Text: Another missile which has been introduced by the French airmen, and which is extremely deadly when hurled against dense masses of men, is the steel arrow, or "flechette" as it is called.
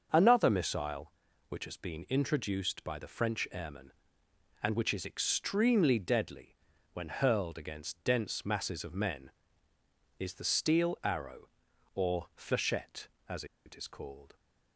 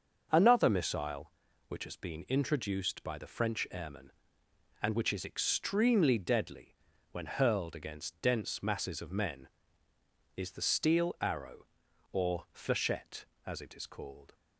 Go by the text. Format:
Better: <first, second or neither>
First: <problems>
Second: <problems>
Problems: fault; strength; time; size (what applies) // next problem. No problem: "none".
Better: second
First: starts louder than the rest; until 1.1 s; 6.5 dB // pauses between "deadly" and "when"; slight; at 6.5 s; 0.36 s long // pauses between "as" and "it"; slight; at 13.4 s; 0.21 s long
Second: starts louder than the rest; until 1.3 s; 6.5 dB // pauses between "deadly" and "when"; slight; at 6.7 s; 0.35 s long